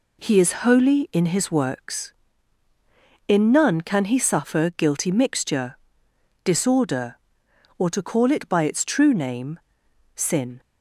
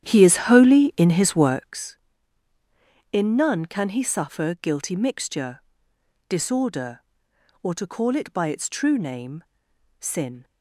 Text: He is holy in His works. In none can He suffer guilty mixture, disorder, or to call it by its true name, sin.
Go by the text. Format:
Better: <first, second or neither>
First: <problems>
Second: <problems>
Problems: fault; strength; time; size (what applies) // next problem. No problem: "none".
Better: first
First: none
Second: starts louder than the rest; strong; until 1.8 s; 10.5 dB